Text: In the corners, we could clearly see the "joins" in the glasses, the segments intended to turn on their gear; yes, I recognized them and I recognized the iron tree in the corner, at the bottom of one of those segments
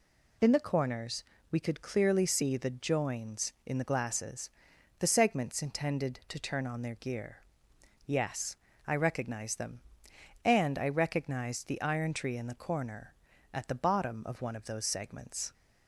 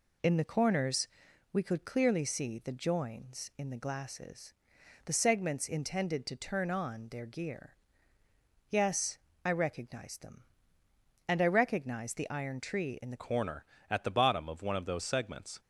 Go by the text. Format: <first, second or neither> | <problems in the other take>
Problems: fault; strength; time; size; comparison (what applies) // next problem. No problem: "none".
first | changes voice at "corner"; from 13.2 s on; 2.3 s long